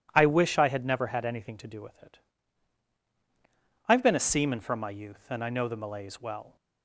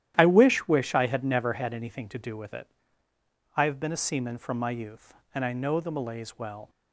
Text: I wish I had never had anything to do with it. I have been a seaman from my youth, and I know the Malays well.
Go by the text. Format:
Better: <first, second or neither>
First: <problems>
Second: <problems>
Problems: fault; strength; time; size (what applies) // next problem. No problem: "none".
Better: first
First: none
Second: starts louder than the rest; strong; until 1.1 s; 12 dB // says "wish" twice; at 0.6 s